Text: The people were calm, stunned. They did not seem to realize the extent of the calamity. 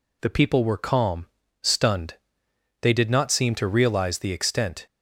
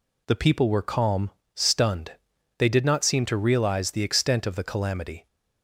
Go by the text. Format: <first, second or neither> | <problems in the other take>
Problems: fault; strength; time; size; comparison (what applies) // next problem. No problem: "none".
second | stops before "of the calamity"; at 4.8 s